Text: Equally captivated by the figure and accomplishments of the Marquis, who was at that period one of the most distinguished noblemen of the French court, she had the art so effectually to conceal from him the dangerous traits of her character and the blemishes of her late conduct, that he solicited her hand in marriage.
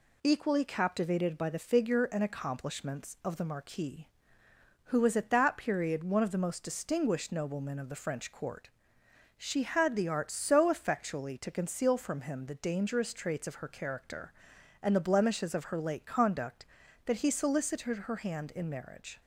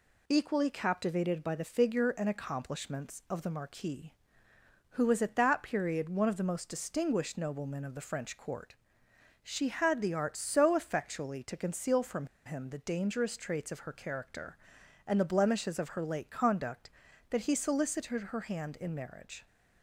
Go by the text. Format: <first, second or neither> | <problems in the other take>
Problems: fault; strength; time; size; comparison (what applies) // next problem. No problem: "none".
first | pauses between "from" and "him"; slight; at 12.2 s; 0.20 s long